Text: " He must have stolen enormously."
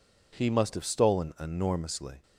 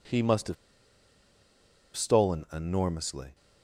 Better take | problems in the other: first | pauses between "have" and "stolen"; strong; at 0.5 s; 1.4 s long

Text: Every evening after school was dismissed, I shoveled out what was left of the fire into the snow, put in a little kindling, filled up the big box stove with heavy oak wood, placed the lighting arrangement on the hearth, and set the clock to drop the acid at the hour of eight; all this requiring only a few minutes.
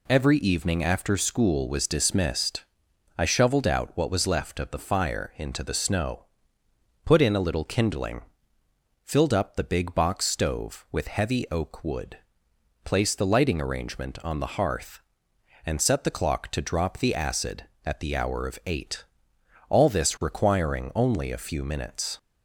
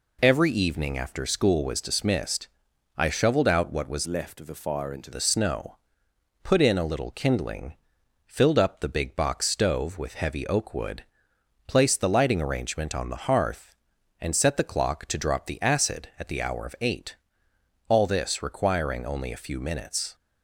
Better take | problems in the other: first | changes voice from "left" to "into"; from 4.0 to 5.1 s; 1.1 s long

